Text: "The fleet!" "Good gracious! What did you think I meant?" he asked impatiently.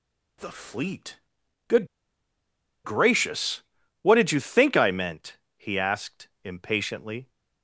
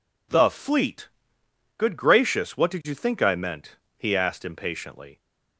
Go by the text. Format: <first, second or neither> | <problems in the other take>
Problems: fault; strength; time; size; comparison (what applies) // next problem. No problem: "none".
second | pauses between "Good" and "gracious"; at 1.8 s; 0.99 s long